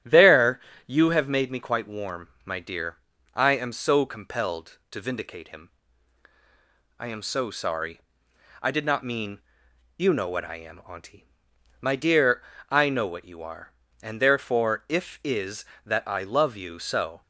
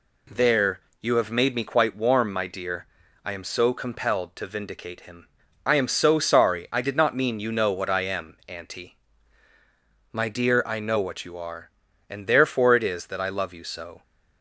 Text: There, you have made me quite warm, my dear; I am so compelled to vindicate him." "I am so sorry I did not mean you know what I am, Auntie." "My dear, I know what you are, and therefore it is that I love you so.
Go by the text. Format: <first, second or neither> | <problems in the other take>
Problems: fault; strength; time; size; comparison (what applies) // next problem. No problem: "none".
second | starts louder than the rest; strong; until 1.3 s; 11 dB // pauses between "sorry" and "I"; noticeable; at 7.9 s; 0.62 s long // pauses between "mean" and "you"; noticeable; at 9.3 s; 0.56 s long // says "if" for "it"; at 14.8 s